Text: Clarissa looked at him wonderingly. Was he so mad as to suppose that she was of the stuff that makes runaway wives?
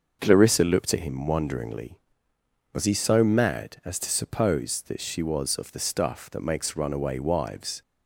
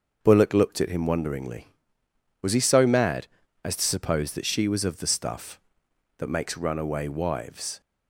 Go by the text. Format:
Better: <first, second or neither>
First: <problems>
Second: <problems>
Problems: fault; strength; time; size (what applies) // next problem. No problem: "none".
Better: first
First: starts louder than the rest; until 1.2 s; 6 dB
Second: starts louder than the rest; until 1.2 s; 6.5 dB // says "Bullock" for "Clarissa"; at 0.2 s